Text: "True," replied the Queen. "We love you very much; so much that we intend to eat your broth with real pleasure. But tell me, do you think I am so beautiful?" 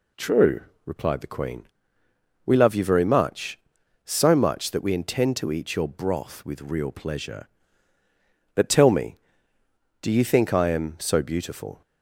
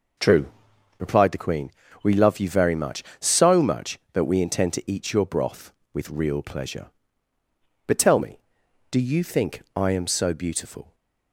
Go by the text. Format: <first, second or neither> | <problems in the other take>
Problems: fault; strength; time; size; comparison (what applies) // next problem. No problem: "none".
neither | none